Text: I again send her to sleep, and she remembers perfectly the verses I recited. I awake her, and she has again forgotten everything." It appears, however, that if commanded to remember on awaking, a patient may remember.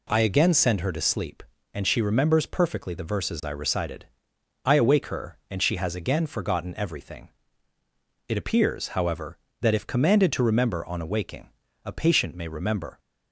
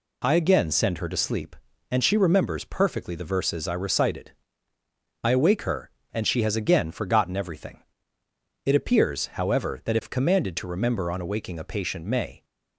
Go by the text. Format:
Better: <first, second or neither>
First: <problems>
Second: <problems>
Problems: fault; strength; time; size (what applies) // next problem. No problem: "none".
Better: first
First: none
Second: stops before "remember"; at 12.4 s